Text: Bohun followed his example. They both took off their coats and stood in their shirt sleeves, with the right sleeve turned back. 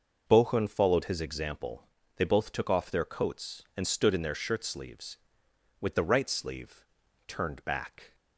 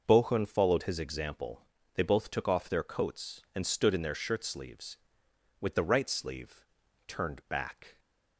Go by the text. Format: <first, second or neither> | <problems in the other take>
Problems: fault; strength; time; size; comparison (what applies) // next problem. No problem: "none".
neither | pauses between "sleeve" and "turned"; the same in both